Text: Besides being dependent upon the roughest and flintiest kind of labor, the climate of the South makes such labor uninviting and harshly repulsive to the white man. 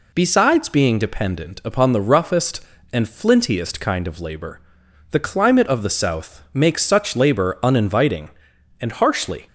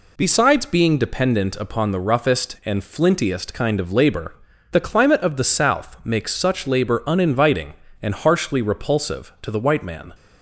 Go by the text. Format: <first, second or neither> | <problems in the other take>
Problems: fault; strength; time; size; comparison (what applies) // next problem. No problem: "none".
second | stops before "repulsive to the white man"; at 9.4 s